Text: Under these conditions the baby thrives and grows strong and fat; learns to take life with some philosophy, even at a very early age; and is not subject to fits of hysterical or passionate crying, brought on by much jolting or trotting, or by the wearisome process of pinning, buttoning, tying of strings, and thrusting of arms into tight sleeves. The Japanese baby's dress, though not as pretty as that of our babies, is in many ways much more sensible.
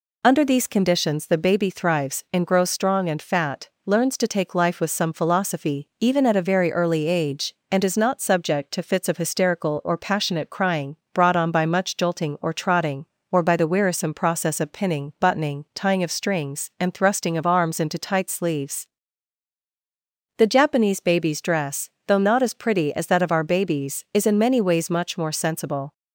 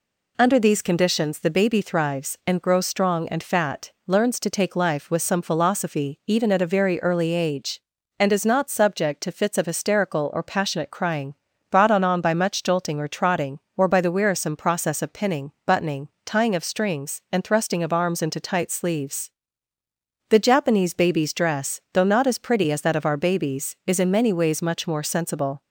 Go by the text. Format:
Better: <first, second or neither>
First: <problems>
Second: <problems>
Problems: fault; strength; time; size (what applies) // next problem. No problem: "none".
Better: first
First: none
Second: says "on" twice; at 12.0 s